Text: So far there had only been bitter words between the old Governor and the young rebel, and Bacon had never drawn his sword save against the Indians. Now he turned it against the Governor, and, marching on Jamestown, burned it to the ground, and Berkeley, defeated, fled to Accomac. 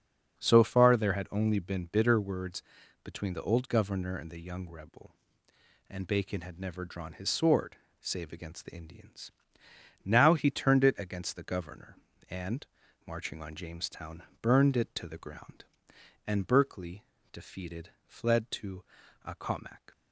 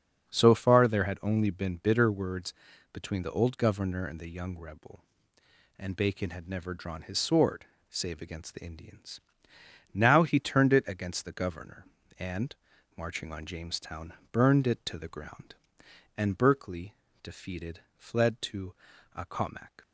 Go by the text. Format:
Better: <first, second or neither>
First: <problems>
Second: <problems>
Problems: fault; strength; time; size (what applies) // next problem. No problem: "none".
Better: neither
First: starts louder than the rest; strong; until 1.4 s; 7 dB // pauses between "words" and "between"; at 2.6 s; 0.40 s long // pauses between "sword" and "save"; slight; at 7.7 s; 0.24 s long // pauses between "to" and "Accomac"; at 18.8 s; 0.42 s long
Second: starts louder than the rest; strong; until 1.3 s; 7 dB // pauses between "words" and "between"; at 2.5 s; 0.38 s long // pauses between "sword" and "save"; slight; at 7.6 s; 0.24 s long // pauses between "to" and "Accomac"; at 18.7 s; 0.42 s long